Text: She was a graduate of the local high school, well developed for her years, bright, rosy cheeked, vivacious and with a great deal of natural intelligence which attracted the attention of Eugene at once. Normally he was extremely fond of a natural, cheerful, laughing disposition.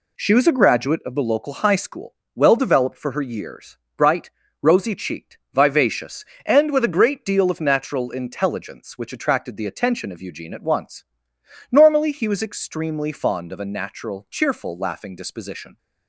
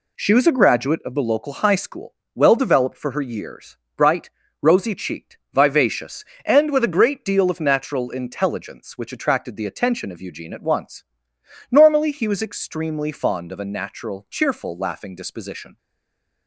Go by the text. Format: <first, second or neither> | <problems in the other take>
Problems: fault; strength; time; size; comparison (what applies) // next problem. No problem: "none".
first | stays silent after the last word; slight; from 15.7 s on; 0.7 s long